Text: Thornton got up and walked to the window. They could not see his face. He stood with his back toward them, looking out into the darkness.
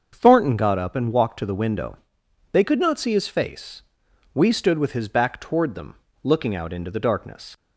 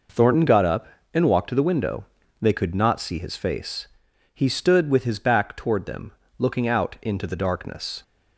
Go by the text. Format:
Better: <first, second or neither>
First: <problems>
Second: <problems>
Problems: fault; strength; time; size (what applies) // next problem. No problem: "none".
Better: second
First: starts louder than the rest; until 1.1 s; 6.5 dB // says "We" for "He"; at 4.3 s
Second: none